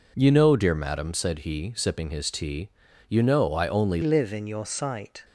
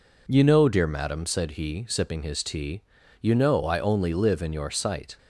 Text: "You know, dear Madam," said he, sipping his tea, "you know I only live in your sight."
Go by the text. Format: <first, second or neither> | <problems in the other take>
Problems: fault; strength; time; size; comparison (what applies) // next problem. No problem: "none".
second | changes voice at "live"; from 4.0 s on; 1.2 s long